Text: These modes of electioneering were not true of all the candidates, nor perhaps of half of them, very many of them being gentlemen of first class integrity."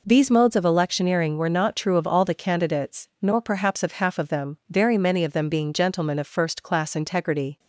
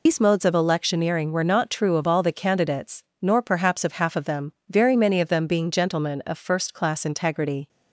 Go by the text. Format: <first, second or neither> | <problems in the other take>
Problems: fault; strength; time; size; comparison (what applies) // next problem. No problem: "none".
first | loses the start of "These"; at 0.0 s; 90 ms